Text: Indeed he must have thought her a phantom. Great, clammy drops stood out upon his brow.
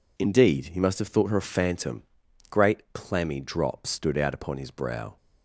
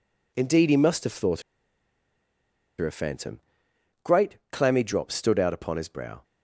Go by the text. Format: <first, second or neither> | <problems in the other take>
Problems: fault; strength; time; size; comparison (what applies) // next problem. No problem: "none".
first | pauses between "thought" and "her"; strong; at 1.4 s; 1.3 s long